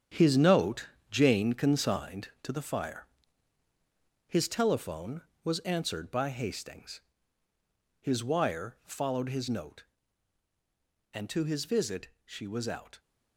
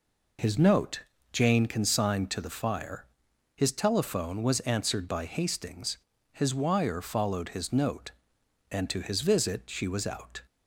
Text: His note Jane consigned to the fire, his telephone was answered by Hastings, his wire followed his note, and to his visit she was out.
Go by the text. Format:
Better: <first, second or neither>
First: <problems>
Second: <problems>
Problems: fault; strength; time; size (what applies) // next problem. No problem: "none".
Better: second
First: gets quieter; strong; throughout; 9.5 dB // pauses between "note" and "Jane"; slight; at 0.8 s; 0.22 s long // pauses between "visit" and "she"; slight; at 12.0 s; 0.16 s long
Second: pauses between "note" and "Jane"; slight; at 1.0 s; 0.32 s long